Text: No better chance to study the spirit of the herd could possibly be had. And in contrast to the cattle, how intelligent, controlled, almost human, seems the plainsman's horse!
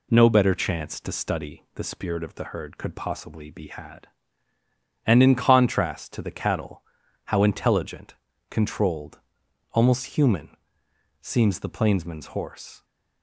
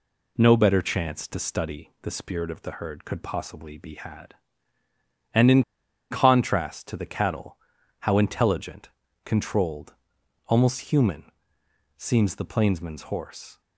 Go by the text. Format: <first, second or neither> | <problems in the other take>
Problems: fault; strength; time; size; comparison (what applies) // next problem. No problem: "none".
first | pauses between "in" and "contrast"; noticeable; at 5.6 s; 0.49 s long